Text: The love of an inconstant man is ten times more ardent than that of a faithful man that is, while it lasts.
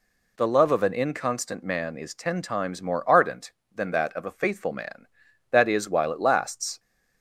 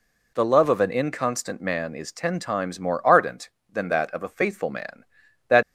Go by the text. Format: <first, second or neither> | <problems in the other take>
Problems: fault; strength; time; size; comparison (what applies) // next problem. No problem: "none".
first | stops before "is while it lasts"; at 5.6 s